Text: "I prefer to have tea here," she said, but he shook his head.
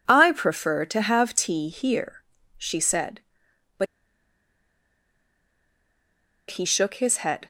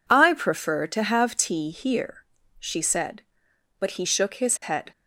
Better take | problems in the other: second | pauses between "but" and "he"; strong; at 3.8 s; 2.6 s long

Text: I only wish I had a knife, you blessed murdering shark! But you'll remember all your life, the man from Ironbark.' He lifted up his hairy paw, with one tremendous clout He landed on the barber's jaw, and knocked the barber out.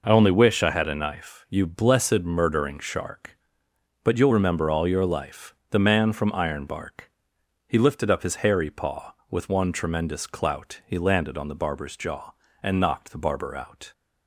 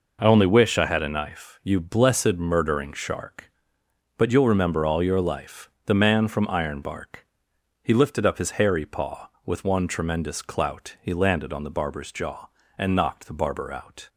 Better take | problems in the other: neither | none

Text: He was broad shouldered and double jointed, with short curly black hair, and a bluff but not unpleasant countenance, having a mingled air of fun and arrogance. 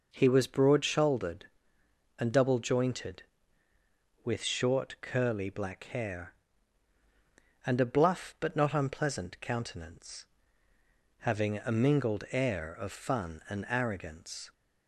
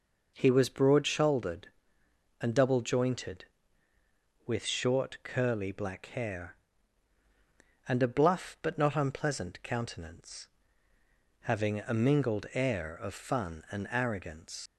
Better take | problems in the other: first | leaves "arrogance" unfinished; at 14.6 s; 85 ms

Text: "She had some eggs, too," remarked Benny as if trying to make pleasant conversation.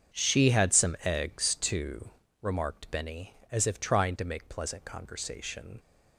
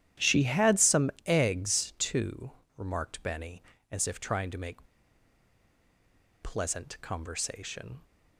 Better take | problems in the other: first | starts louder than the rest; strong; until 1.3 s; 11 dB; strong in the first // pauses between "make" and "pleasant"; strong; at 4.8 s; 1.5 s long

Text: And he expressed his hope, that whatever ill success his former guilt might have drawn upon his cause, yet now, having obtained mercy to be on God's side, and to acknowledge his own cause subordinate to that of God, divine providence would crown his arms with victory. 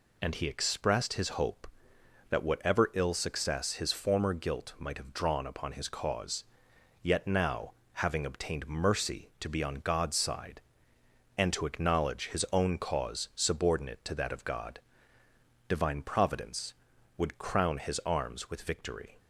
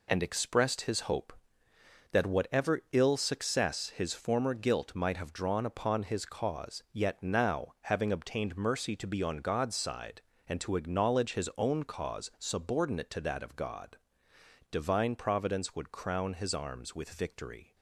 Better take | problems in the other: first | skips "he"; at 0.2 s

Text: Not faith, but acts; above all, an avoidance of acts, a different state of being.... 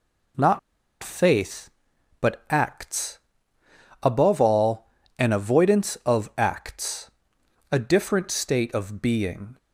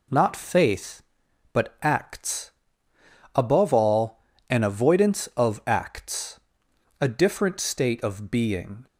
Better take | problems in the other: second | pauses between "Not" and "faith"; at 0.5 s; 0.43 s long

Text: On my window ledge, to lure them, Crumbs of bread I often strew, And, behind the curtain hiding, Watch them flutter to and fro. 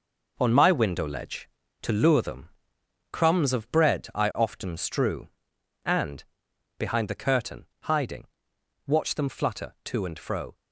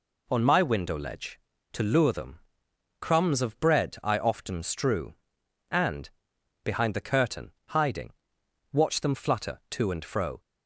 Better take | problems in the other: second | gets quieter; strong; throughout; 7.5 dB // pauses between "curtain" and "hiding"; slight; at 7.6 s; 0.16 s long; slight in the second

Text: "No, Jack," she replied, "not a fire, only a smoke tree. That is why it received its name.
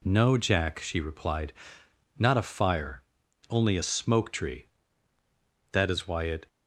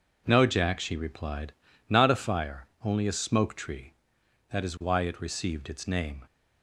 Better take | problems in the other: second | stops before "received its name"; at 6.4 s

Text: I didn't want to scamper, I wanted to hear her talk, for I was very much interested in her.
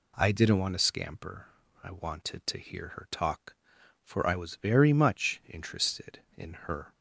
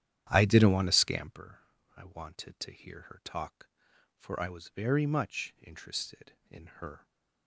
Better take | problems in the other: first | starts louder than the rest; strong; until 1.4 s; 10.5 dB

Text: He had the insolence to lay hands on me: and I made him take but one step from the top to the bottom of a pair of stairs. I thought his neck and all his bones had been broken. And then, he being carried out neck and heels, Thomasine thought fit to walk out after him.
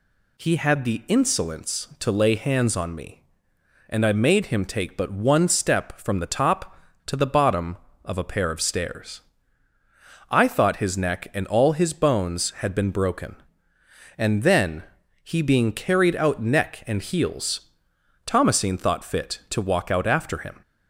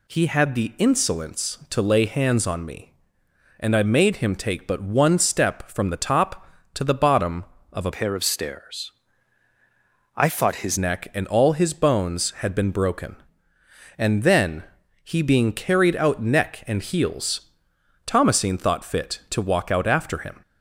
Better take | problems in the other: first | changes voice from "pair" to "his"; from 7.9 to 10.7 s; 2.8 s long

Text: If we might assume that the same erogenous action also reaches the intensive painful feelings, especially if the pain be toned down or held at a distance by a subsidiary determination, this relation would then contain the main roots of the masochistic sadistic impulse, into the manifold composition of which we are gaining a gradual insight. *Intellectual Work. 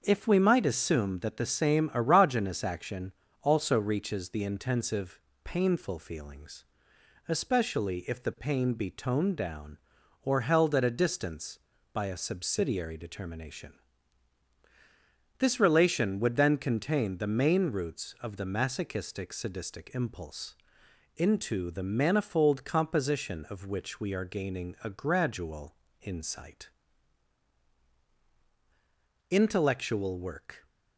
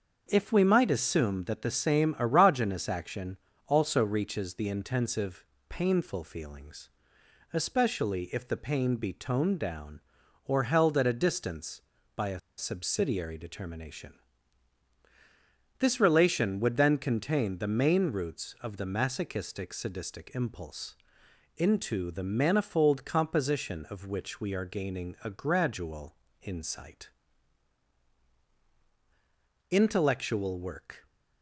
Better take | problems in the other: first | starts louder than the rest; until 1.2 s; 6.5 dB; also in the first // pauses between "action" and "also"; slight; at 3.3 s; 0.32 s long; slight in the first // pauses between "intensive" and "painful"; slight; at 5.4 s; 0.24 s long; slight in the first // pauses between "a" and "subsidiary"; slight; at 12.3 s; 0.18 s long // pauses between "gradual" and "insight"; slight; at 26.1 s; 0.26 s long; slight in the first

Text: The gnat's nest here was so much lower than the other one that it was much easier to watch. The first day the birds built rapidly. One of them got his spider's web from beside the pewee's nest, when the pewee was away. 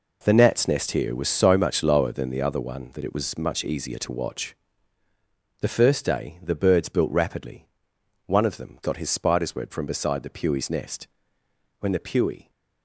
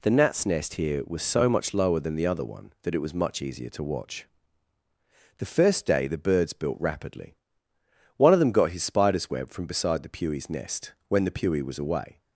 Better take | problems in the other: second | stops before "was away"; at 12.4 s

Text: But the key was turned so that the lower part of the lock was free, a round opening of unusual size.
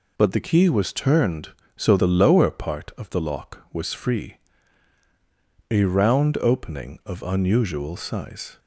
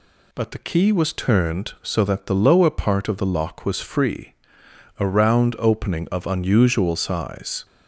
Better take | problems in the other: second | skips "that"; at 1.9 s

